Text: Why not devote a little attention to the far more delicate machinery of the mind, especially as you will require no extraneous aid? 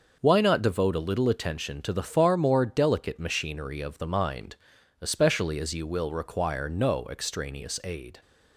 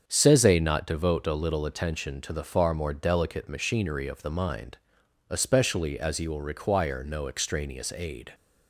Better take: first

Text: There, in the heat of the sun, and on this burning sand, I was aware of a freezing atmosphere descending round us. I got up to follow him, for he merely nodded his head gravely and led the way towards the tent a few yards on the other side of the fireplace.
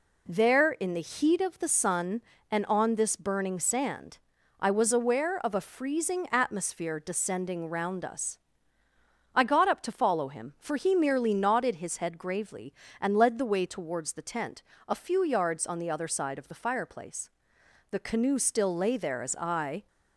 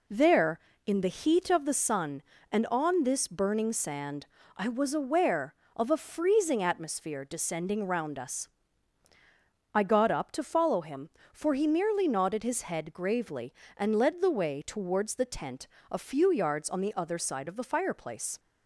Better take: second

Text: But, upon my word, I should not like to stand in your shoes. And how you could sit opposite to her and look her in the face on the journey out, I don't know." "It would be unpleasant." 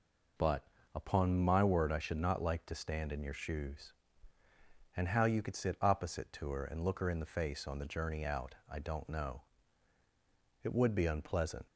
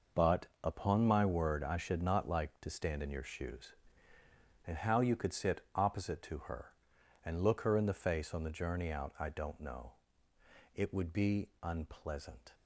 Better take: first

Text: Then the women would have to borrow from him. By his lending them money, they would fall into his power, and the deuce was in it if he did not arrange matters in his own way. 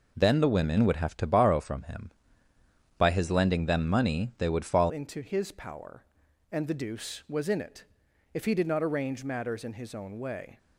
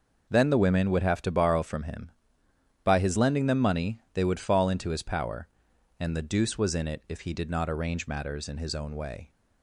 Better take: second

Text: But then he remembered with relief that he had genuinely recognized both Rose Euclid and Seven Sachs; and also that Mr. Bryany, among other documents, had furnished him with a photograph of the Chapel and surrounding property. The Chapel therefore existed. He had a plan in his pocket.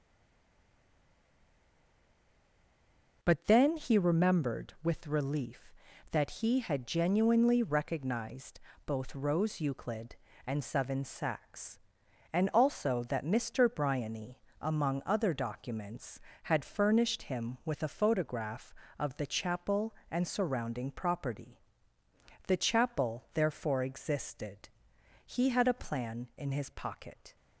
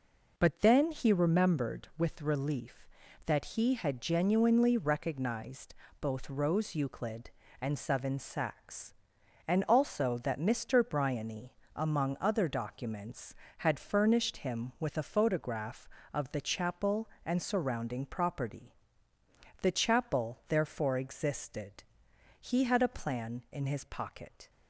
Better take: second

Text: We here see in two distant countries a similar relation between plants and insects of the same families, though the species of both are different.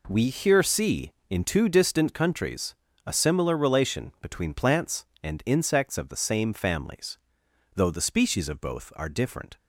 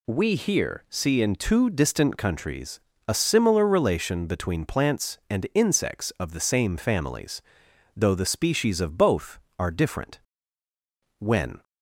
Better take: first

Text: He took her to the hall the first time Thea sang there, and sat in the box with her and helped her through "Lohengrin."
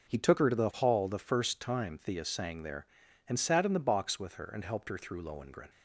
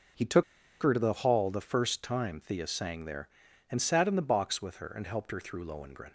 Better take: first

